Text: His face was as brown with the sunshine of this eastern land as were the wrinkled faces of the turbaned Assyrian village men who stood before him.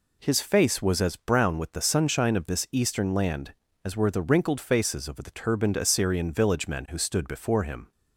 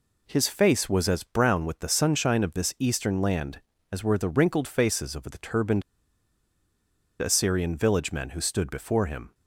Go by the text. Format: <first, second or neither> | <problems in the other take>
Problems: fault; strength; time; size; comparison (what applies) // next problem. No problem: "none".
first | pauses between "turbaned" and "Assyrian"; strong; at 5.8 s; 1.3 s long